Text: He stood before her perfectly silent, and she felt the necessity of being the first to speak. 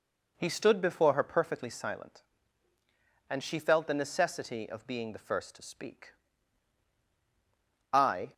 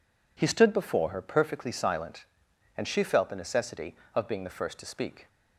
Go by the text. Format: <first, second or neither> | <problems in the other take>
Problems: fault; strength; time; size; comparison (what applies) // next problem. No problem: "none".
second | goes on to say "I"; slight; from 7.9 s on; 0.40 s long